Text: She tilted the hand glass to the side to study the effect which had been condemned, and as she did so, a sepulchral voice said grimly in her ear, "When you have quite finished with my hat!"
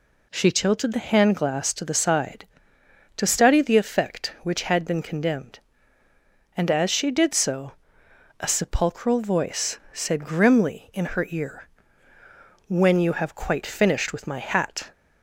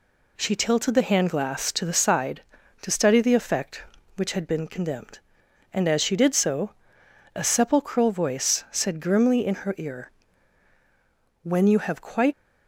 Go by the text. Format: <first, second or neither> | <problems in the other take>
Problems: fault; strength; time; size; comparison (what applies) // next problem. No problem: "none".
first | stops before "finished with my hat"; at 12.3 s